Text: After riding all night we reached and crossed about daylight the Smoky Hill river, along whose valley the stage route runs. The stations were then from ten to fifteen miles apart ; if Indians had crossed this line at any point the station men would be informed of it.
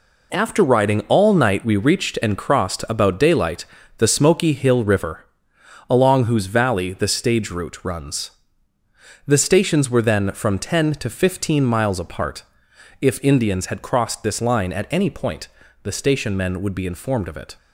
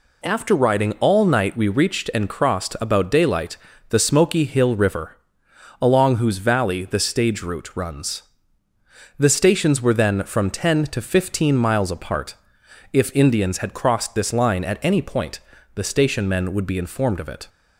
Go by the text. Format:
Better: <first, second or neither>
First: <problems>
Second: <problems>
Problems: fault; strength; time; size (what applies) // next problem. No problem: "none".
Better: second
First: gets quieter; strong; throughout; 8.5 dB // pauses between "daylight" and "the"; slight; at 3.6 s; 0.32 s long // pauses between "point" and "the"; slight; at 15.4 s; 0.34 s long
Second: pauses between "daylight" and "the"; slight; at 3.5 s; 0.32 s long // pauses between "point" and "the"; slight; at 15.3 s; 0.34 s long